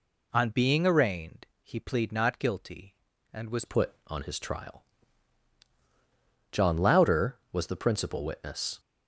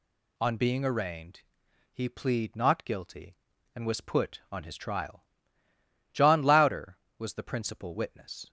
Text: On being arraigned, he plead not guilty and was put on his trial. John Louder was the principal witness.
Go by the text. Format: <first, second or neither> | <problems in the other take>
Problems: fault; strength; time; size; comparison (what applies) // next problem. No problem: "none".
second | changes voice at "put"; from 3.6 s on; 5.1 s long